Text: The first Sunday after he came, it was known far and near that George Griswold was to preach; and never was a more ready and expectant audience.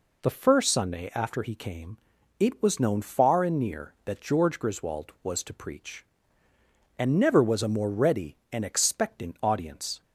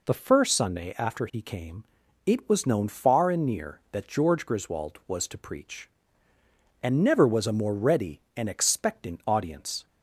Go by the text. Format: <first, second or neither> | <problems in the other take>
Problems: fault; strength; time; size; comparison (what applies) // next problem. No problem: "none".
neither | none